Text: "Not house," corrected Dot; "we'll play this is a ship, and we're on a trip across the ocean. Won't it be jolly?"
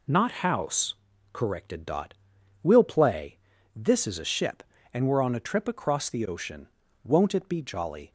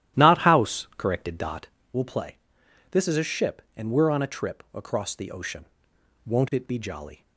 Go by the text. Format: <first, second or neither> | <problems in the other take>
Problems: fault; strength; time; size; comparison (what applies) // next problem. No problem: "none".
first | starts louder than the rest; strong; until 1.9 s; 13 dB // pauses between "play" and "this"; noticeable; at 2.3 s; 0.54 s long; also in the first